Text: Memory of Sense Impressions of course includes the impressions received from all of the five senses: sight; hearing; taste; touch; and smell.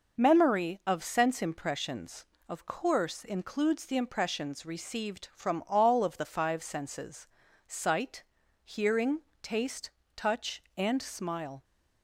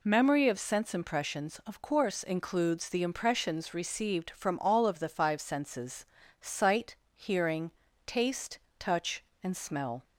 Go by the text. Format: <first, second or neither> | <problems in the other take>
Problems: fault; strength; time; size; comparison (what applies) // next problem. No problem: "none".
second | says "smile" for "smell"; at 11.0 s